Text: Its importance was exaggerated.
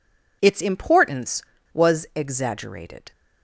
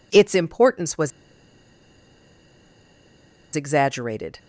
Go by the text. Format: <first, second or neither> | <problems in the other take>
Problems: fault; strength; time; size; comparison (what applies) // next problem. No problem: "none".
first | pauses between "was" and "exaggerated"; strong; at 1.1 s; 2.4 s long